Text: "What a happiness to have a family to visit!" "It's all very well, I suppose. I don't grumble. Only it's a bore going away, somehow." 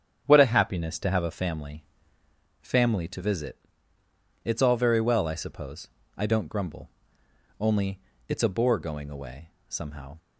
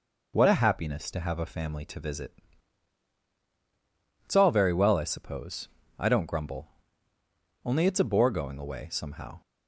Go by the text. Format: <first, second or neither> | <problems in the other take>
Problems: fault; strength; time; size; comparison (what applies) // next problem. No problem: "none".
second | starts louder than the rest; strong; until 1.2 s; 9 dB // says "family" twice; at 2.6 s // pauses between "Only" and "it's"; slight; at 7.9 s; 0.30 s long